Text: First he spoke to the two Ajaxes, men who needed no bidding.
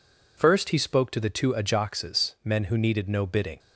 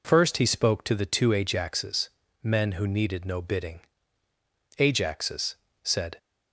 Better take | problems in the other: first | goes on to say "Ajaxes said"; from 4.7 s on; 1.4 s long

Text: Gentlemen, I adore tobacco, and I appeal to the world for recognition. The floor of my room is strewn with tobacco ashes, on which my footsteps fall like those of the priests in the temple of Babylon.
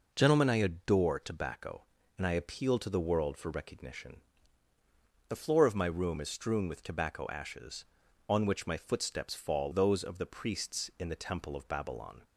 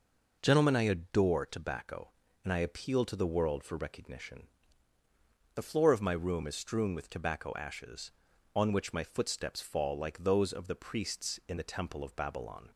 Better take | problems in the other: second | skips "like"; at 9.7 s

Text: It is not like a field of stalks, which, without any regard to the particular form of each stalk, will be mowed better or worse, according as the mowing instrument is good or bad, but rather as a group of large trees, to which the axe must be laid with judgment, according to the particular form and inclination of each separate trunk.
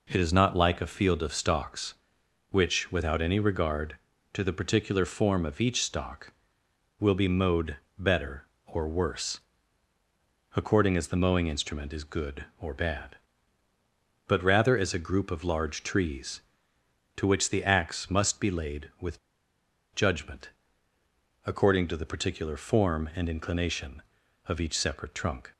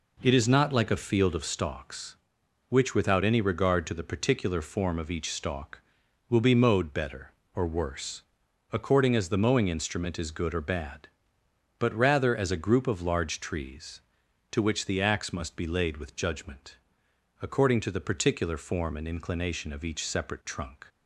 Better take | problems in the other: second | pauses between "mowed" and "better"; slight; at 7.7 s; 0.22 s long // pauses between "with" and "judgment"; noticeable; at 19.1 s; 0.75 s long

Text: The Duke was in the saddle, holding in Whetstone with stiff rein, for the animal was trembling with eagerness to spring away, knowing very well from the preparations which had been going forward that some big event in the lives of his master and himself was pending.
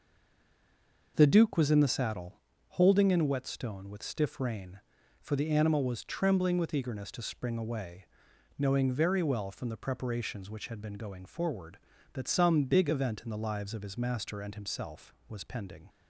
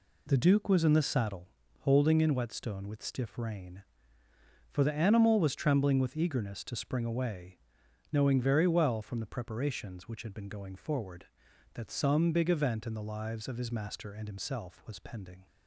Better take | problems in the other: second | stays silent before the first word; until 1.1 s; 1.1 s long

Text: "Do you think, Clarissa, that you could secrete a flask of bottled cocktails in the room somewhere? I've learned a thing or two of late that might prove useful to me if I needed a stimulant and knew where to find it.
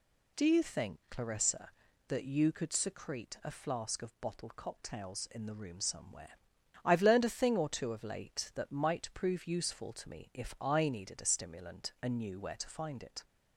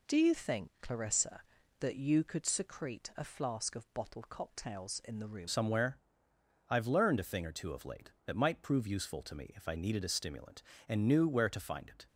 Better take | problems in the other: first | changes voice at "somewhere"; from 5.4 s on; 6.6 s long

